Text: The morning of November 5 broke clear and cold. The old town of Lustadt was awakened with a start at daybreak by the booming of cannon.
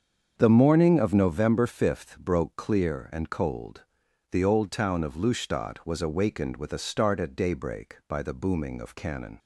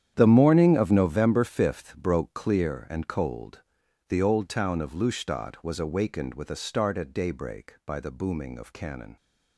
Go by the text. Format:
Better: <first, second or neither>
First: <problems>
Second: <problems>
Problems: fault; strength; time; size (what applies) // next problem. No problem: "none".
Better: first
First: starts louder than the rest; strong; until 1.3 s; 7.5 dB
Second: gets quieter; strong; throughout; 13.5 dB // starts louder than the rest; strong; until 1.1 s; 9.5 dB